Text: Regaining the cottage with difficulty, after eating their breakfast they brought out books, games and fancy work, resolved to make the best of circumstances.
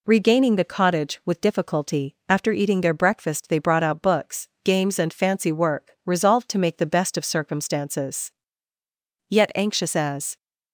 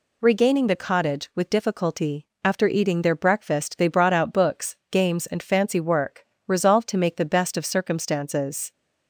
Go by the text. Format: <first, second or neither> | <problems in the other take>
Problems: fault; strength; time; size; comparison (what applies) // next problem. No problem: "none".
second | goes on to say "Yet anxious as"; noticeable; from 9.3 s on; 1.0 s long